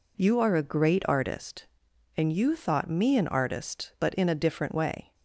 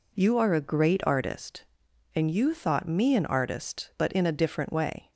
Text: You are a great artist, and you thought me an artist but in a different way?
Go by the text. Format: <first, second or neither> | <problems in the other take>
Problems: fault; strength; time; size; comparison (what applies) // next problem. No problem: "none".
neither | none